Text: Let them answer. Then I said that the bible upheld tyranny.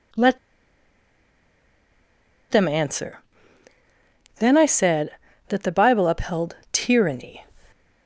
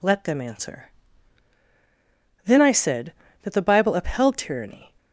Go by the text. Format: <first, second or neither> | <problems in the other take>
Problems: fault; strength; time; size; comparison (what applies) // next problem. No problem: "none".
second | pauses between "Let" and "them"; strong; at 0.3 s; 2.1 s long // pauses between "upheld" and "tyranny"; slight; at 6.5 s; 0.16 s long